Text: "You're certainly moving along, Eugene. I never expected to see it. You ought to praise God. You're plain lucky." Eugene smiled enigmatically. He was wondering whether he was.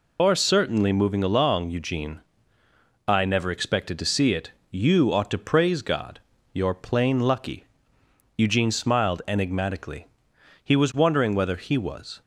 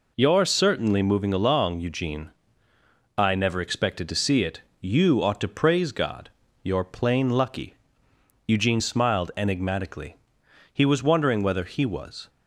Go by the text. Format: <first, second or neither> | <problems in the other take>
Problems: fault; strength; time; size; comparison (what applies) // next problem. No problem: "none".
second | loses the start of "You're"; at 0.1 s; 140 ms